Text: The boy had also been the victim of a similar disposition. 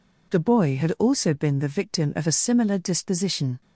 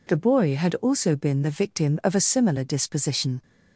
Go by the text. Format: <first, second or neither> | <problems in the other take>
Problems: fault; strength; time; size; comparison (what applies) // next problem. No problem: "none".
neither | none